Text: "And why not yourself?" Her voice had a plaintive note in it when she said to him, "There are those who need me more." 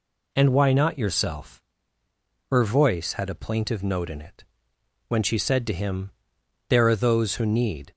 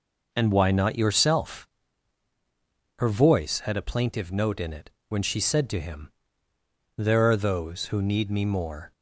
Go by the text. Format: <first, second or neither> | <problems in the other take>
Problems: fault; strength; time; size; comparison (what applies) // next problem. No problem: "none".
second | pauses between "it" and "when"; noticeable; at 4.4 s; 0.62 s long; slight in the second // stops before "me more"; at 7.9 s